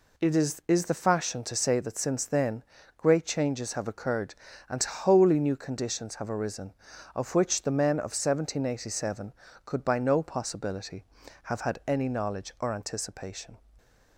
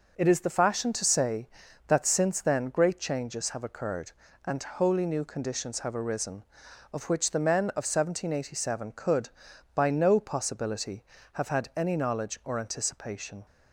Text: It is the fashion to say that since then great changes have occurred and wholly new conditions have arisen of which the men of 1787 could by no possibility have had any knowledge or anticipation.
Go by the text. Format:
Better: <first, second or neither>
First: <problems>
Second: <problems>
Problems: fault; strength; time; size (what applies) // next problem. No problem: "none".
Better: second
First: says "is" twice; at 0.6 s // pauses between "then" and "great"; slight; at 2.6 s; 0.32 s long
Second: none